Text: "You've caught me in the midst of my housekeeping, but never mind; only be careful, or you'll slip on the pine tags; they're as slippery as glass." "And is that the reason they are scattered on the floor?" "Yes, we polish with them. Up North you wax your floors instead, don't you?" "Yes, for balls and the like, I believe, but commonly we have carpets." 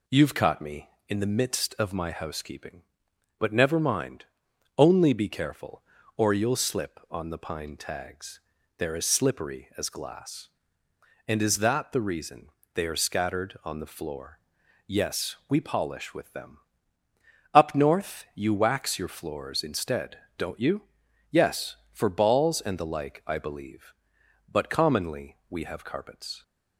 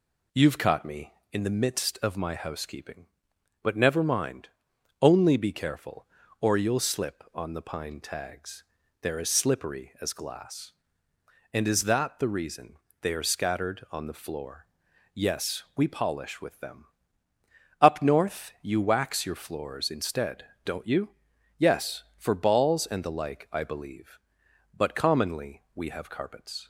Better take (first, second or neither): neither